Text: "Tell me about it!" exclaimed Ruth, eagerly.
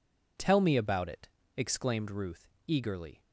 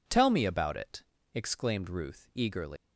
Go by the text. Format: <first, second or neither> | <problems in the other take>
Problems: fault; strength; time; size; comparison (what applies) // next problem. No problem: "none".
first | leaves "eagerly" unfinished; at 2.7 s; 175 ms